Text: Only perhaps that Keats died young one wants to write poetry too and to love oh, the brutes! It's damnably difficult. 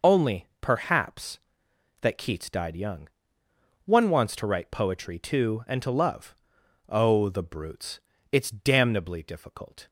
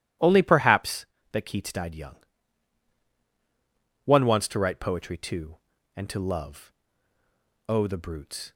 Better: first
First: pauses between "young" and "one"; noticeable; at 3.0 s; 0.76 s long // pauses between "love" and "oh"; noticeable; at 6.3 s; 0.54 s long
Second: pauses between "young" and "one"; strong; at 2.1 s; 1.9 s long // pauses between "love" and "oh"; noticeable; at 6.7 s; 0.96 s long // stops before "It's damnably difficult"; at 8.5 s

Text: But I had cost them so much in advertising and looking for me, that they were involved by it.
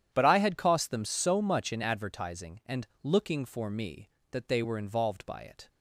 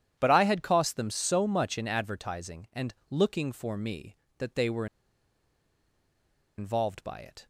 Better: first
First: starts louder than the rest; strong; until 1.1 s; 10 dB // pauses between "and" and "looking"; slight; at 2.8 s; 0.16 s long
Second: starts louder than the rest; strong; until 1.2 s; 10 dB // pauses between "and" and "looking"; slight; at 2.9 s; 0.16 s long // pauses between "were" and "involved"; strong; at 4.8 s; 1.7 s long

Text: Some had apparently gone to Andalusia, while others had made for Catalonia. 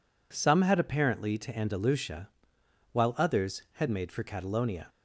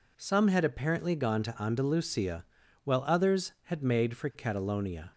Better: second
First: skips "gone"; at 1.3 s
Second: none

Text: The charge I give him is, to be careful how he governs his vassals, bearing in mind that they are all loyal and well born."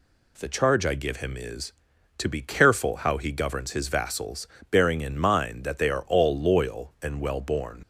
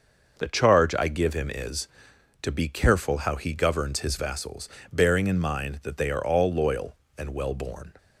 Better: second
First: leaves "born" unfinished; at 7.8 s; 85 ms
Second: none

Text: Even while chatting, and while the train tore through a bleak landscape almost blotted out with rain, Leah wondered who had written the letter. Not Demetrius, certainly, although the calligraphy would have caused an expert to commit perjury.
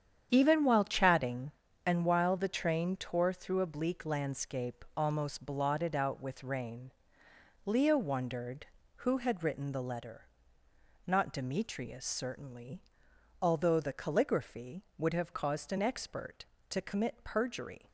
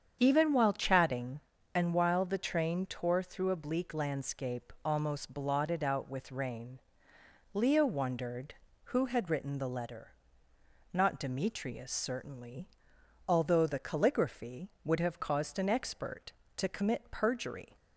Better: second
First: gets quieter; strong; throughout; 9.5 dB // starts louder than the rest; strong; until 1.3 s; 8.5 dB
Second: starts louder than the rest; strong; until 1.2 s; 8 dB

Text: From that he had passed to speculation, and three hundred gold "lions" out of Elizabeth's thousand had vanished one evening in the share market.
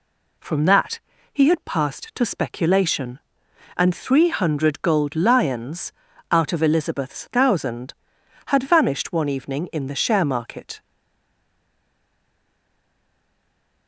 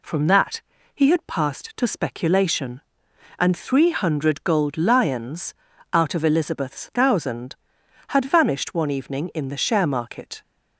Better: second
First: pauses between "that" and "he"; slight; at 0.9 s; 0.34 s long // pauses between "lions" and "out"; at 5.9 s; 0.38 s long // stays silent after the last word; strong; from 10.8 s on; 3.0 s long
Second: pauses between "that" and "he"; slight; at 0.6 s; 0.34 s long // pauses between "lions" and "out"; at 5.5 s; 0.38 s long

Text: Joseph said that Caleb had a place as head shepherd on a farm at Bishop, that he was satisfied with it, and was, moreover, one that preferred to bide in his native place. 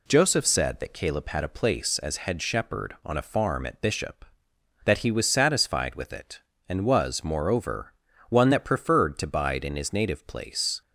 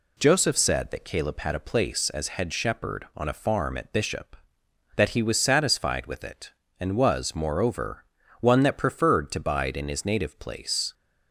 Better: neither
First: none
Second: none

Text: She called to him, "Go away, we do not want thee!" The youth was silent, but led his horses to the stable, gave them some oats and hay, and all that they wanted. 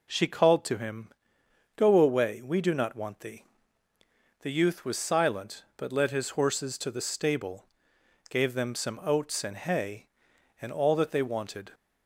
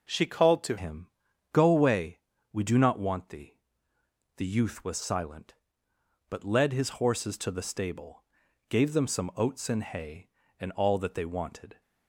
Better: first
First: none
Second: changes voice at "him"; from 0.7 s on; 11.1 s long

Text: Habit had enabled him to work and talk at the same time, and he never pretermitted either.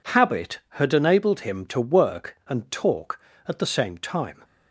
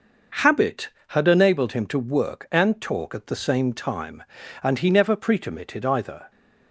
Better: second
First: stops before "and he never pretermitted either"; at 4.4 s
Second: none

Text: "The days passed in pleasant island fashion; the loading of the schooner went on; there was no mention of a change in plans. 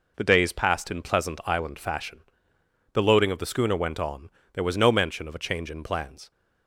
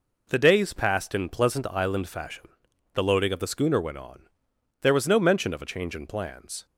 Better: neither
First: none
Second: none

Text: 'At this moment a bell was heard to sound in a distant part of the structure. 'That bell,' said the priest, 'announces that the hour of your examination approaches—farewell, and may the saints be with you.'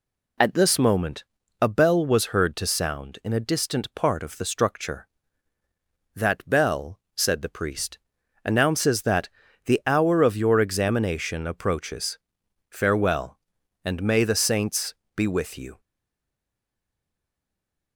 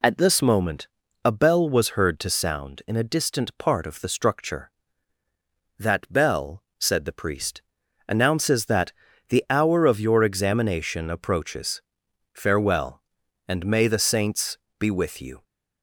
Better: second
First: pauses between "moment" and "a"; slight; at 1.2 s; 0.36 s long // pauses between "that" and "the"; at 9.2 s; 0.38 s long // pauses between "saints" and "be"; slight; at 14.9 s; 0.22 s long // stays silent after the last word; from 15.7 s on; 2.2 s long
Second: pauses between "moment" and "a"; slight; at 0.8 s; 0.36 s long // pauses between "that" and "the"; at 8.9 s; 0.38 s long // pauses between "saints" and "be"; slight; at 14.5 s; 0.22 s long

